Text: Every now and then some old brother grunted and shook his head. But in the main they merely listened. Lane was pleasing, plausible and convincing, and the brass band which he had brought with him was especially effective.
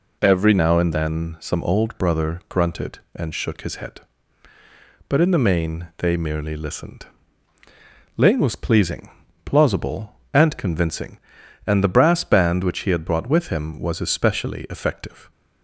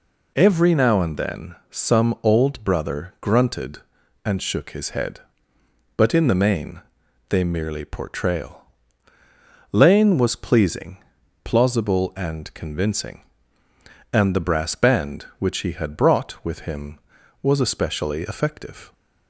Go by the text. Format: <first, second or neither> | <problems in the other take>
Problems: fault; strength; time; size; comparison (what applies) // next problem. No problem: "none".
first | pauses between "main" and "they"; noticeable; at 6.8 s; 0.48 s long // says "portrayal" for "listened"; at 7.8 s